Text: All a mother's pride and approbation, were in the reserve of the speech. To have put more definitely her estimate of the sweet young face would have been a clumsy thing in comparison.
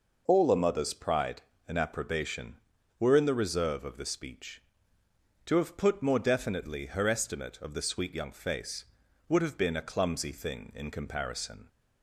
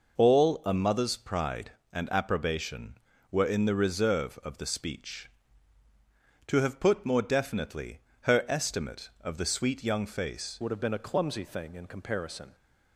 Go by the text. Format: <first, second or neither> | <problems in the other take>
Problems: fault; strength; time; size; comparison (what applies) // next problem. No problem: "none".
first | pauses between "definitely" and "her"; slight; at 8.0 s; 0.20 s long // changes voice at "would"; from 10.6 s on; 1.9 s long